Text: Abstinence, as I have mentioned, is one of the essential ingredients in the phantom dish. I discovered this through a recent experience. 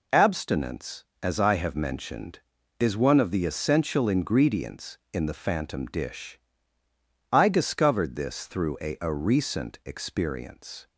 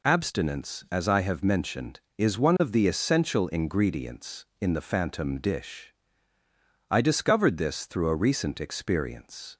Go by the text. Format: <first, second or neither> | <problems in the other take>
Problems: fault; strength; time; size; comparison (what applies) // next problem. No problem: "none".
second | says "a" twice; at 9.0 s